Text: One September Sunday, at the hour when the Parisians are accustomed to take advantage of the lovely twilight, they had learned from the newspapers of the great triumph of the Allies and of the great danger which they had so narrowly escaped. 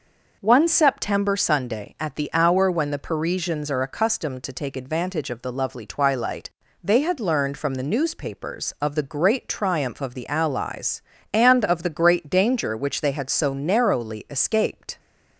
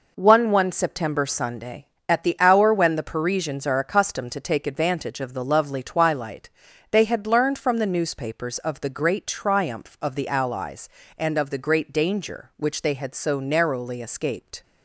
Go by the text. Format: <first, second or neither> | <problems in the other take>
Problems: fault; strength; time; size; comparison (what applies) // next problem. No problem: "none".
first | says "One" twice; at 0.5 s